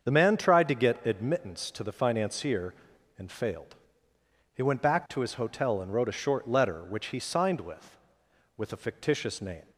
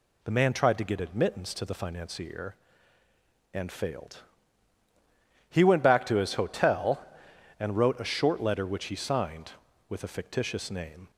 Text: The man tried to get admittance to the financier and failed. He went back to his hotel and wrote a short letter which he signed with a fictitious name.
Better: second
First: starts louder than the rest; until 1.0 s; 7 dB // says "with" twice; at 8.5 s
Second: none

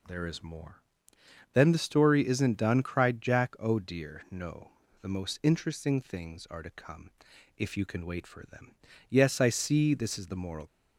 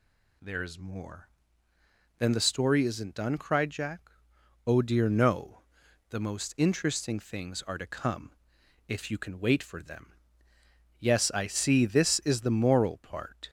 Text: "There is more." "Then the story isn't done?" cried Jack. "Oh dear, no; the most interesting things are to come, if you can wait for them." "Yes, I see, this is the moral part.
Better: second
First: stops before "part"; at 10.6 s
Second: none

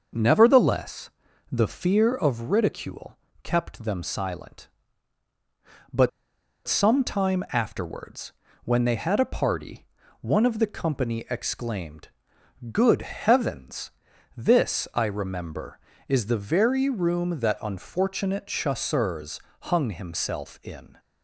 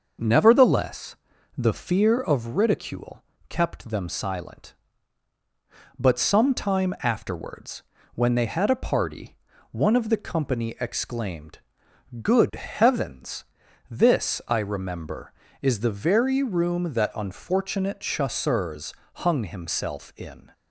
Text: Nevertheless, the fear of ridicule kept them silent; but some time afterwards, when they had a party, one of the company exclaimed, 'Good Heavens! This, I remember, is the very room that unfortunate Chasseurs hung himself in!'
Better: second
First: starts louder than the rest; noticeable; until 1.5 s; 6 dB // pauses between "ridicule" and "kept"; slight; at 3.1 s; 0.24 s long // pauses between "but" and "some"; noticeable; at 6.0 s; 0.57 s long // pauses between "Chasseurs" and "hung"; slight; at 19.3 s; 0.22 s long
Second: starts louder than the rest; noticeable; until 1.6 s; 6 dB // pauses between "ridicule" and "kept"; slight; at 3.2 s; 0.24 s long // pauses between "Chasseurs" and "hung"; slight; at 18.9 s; 0.22 s long

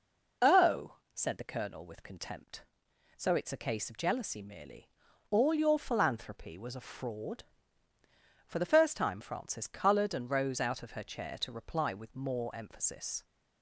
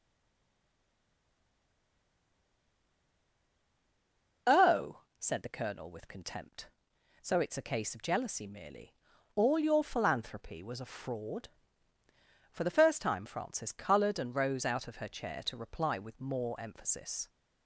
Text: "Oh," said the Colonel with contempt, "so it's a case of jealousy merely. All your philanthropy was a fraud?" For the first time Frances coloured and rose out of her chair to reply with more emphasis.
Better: first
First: none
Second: stays silent before the first word; strong; until 4.4 s; 4.4 s long

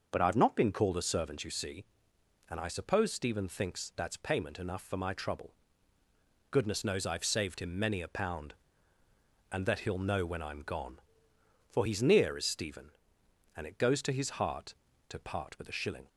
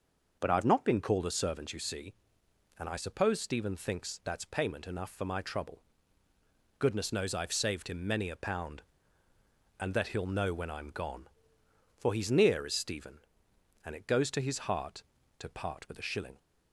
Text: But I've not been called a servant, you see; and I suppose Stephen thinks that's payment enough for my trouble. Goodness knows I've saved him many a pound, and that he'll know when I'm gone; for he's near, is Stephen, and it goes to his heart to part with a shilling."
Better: neither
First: starts louder than the rest; until 1.1 s; 6 dB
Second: starts louder than the rest; noticeable; until 1.4 s; 6 dB

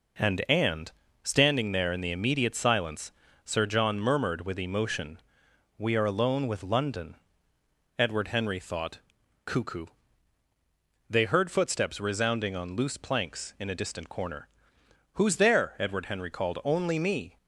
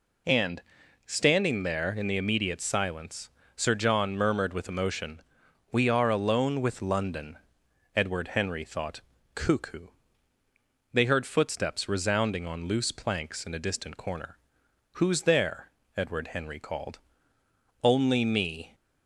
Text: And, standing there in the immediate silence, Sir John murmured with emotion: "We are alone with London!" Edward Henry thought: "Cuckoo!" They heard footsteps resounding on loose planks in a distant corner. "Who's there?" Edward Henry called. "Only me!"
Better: second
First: says "And" twice; at 0.4 s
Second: none

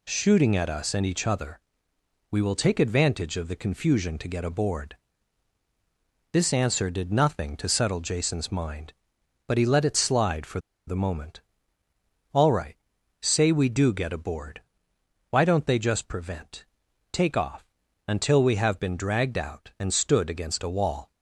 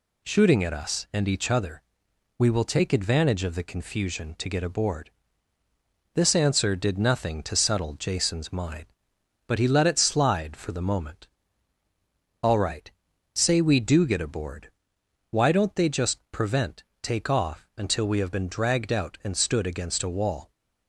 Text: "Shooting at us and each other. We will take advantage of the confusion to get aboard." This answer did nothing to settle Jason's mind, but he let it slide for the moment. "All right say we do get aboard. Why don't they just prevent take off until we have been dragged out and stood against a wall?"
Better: second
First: pauses between "for" and "the"; slight; at 10.5 s; 0.28 s long // pauses between "right" and "say"; noticeable; at 12.7 s; 0.46 s long // pauses between "prevent" and "take"; noticeable; at 16.6 s; 0.48 s long // pauses between "off" and "until"; at 17.6 s; 0.42 s long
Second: pauses between "right" and "say"; at 12.8 s; 0.44 s long // pauses between "prevent" and "take"; slight; at 16.8 s; 0.18 s long

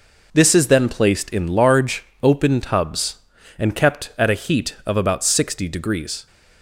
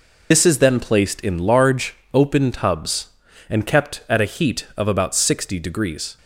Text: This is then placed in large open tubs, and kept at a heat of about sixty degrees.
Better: first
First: pauses between "large" and "open"; slight; at 2.0 s; 0.18 s long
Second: loses the start of "This"; at 0.3 s; 75 ms // pauses between "large" and "open"; slight; at 1.9 s; 0.18 s long

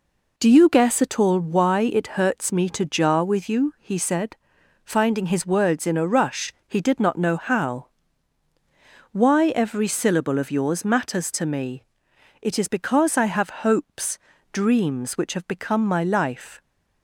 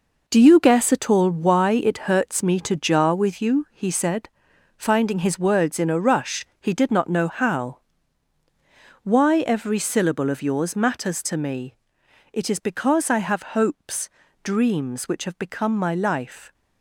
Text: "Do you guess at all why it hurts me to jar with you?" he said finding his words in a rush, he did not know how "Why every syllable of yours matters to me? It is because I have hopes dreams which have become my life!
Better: first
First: pauses between "said" and "finding"; noticeable; at 4.3 s; 0.48 s long // pauses between "how" and "Why"; strong; at 7.8 s; 1.2 s long // pauses between "hopes" and "dreams"; slight; at 14.1 s; 0.36 s long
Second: gets quieter; strong; throughout; 9 dB // pauses between "said" and "finding"; noticeable; at 4.2 s; 0.48 s long // pauses between "how" and "Why"; strong; at 7.7 s; 1.2 s long // pauses between "hopes" and "dreams"; slight; at 14.0 s; 0.36 s long

